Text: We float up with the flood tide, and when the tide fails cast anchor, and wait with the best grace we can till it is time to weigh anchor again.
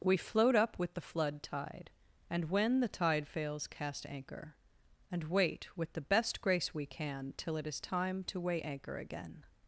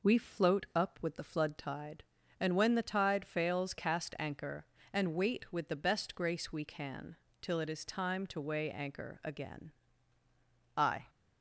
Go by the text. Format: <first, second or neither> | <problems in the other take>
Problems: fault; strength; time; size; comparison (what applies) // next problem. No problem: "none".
first | pauses between "can" and "till"; slight; at 7.1 s; 0.24 s long // goes on to say "I"; slight; from 10.7 s on; 0.30 s long